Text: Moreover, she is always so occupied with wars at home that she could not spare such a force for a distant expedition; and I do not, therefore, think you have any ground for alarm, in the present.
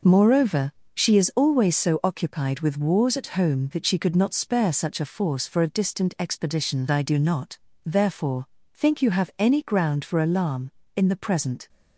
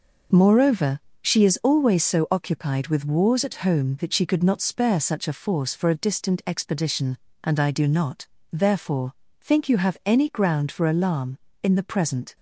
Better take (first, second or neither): second